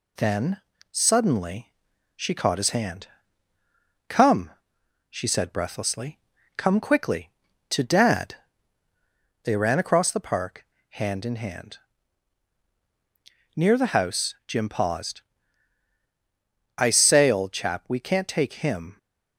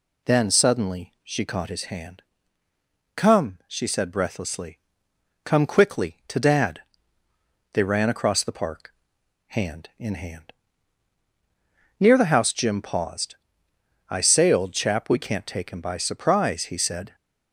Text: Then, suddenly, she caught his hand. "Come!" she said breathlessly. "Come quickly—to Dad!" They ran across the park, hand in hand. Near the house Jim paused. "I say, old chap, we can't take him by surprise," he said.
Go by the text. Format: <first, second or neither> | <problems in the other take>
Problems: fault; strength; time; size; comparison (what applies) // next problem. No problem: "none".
second | stops before "by surprise he said"; at 18.9 s